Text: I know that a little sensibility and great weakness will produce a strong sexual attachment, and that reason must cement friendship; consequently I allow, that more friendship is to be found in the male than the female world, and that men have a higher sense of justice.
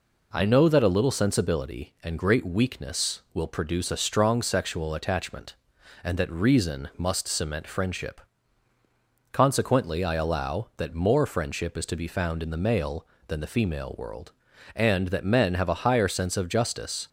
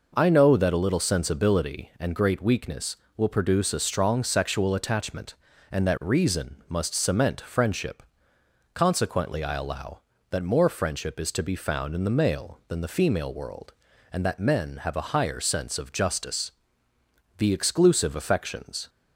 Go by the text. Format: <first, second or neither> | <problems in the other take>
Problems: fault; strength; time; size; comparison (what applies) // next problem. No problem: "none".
first | goes on to say "The exclusive affections"; from 17.3 s on; 1.5 s long